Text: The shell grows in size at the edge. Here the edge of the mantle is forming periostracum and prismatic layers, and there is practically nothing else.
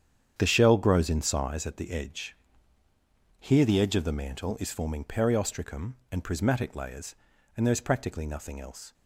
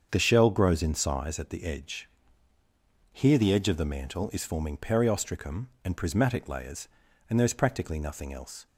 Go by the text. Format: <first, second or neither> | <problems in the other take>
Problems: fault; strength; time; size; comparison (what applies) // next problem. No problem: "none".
second | gets quieter; strong; throughout; 11 dB // starts louder than the rest; strong; until 1.3 s; 8.5 dB; strong in the second